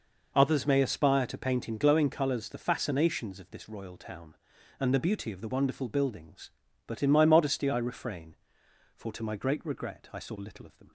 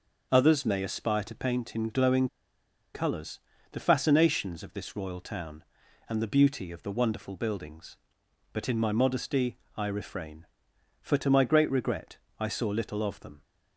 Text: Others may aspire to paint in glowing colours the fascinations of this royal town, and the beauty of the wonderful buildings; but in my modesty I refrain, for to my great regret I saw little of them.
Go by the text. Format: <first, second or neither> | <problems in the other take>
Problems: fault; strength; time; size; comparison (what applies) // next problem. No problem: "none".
first | starts louder than the rest; until 1.3 s; 6.5 dB // pauses between "glowing" and "colours"; noticeable; at 2.2 s; 0.66 s long // pauses between "colours" and "the"; slight; at 3.3 s; 0.34 s long // pauses between "modesty" and "I"; slight; at 9.5 s; 0.18 s long // pauses between "regret" and "I"; slight; at 12.1 s; 0.24 s long